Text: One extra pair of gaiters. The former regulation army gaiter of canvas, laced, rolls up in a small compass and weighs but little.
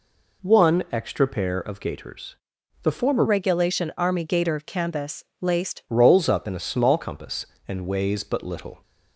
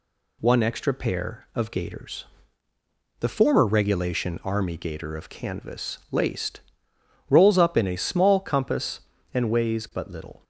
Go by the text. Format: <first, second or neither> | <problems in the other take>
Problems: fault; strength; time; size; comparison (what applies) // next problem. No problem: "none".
second | changes voice from "regulation" to "laced"; from 3.2 to 5.8 s; 2.6 s long